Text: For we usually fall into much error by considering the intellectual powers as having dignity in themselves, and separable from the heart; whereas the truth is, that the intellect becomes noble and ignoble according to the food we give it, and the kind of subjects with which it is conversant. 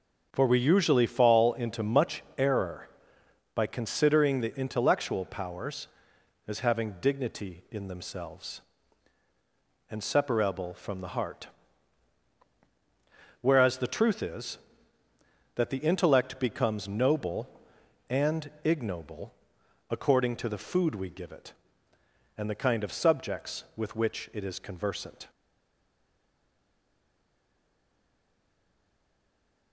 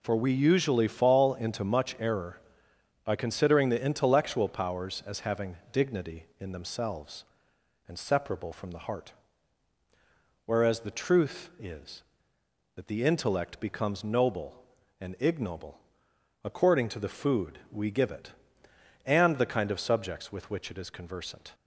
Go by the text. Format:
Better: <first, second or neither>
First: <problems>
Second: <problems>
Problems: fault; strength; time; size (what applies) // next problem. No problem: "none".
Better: second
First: starts louder than the rest; noticeable; until 1.3 s; 6 dB // pauses between "ignoble" and "according"; noticeable; at 19.3 s; 0.56 s long // stays silent after the last word; strong; from 25.3 s on; 4.4 s long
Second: pauses between "ignoble" and "according"; noticeable; at 15.7 s; 0.66 s long